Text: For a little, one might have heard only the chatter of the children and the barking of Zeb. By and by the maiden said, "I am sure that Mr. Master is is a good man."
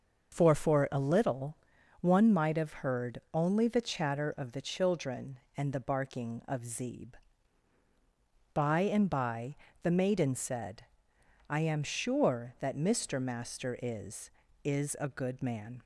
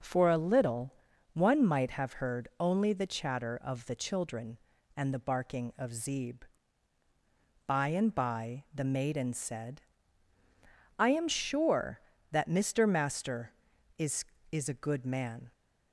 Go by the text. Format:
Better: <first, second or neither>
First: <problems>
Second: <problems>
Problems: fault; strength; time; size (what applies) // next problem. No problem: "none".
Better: second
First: starts louder than the rest; until 1.3 s; 6 dB // says "For" twice; at 0.5 s // pauses between "by" and "the"; slight; at 9.5 s; 0.28 s long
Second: none